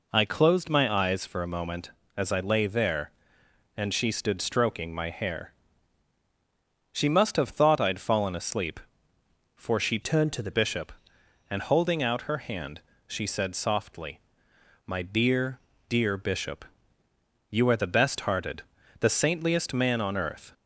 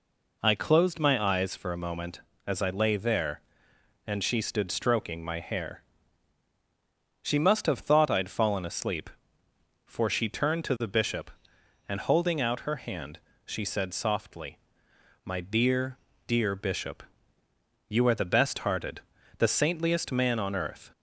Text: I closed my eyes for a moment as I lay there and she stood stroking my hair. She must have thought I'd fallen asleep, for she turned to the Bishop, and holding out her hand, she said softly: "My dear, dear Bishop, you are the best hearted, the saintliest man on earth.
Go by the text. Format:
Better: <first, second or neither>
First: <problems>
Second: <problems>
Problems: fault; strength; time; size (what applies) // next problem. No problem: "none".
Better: second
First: changes voice from "turned" to "the"; from 10.0 to 10.5 s; 0.5 s long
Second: none